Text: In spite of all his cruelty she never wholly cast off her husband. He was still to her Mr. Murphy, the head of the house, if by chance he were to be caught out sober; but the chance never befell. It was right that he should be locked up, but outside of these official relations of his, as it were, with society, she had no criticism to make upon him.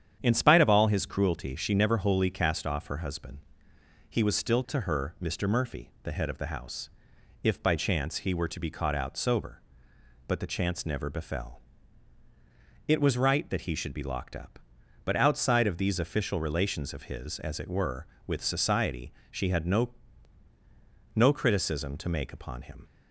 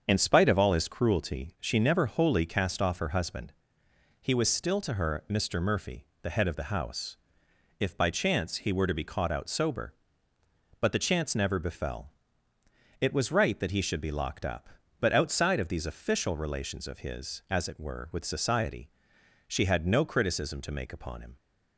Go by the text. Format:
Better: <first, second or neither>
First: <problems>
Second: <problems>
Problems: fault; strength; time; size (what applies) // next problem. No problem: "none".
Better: second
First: starts louder than the rest; strong; until 1.2 s; 9 dB // says "no" twice; at 21.1 s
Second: starts louder than the rest; until 1.0 s; 7 dB